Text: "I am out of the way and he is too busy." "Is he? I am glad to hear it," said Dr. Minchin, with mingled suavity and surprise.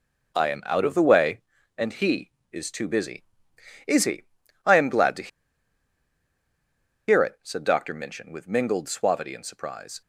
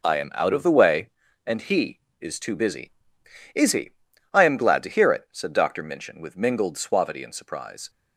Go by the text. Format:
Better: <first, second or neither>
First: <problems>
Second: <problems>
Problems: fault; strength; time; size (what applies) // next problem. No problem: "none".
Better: second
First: pauses between "to" and "hear"; strong; at 5.2 s; 1.8 s long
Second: none